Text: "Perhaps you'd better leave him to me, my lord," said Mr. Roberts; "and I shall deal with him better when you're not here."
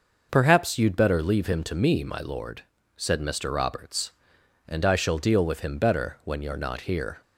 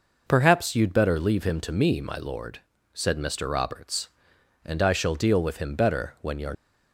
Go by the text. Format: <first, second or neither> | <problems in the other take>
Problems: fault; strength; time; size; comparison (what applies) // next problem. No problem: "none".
first | stops before "not here"; at 6.5 s